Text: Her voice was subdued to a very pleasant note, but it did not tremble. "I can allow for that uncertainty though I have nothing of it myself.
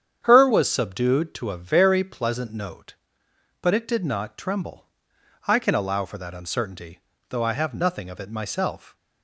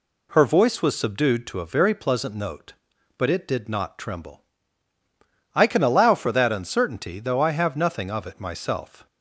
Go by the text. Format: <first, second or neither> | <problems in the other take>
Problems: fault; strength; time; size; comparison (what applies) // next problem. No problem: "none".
second | starts louder than the rest; strong; until 1.2 s; 8.5 dB // skips "voice"; at 0.4 s // pauses between "uncertainty" and "though"; slight; at 6.9 s; 0.30 s long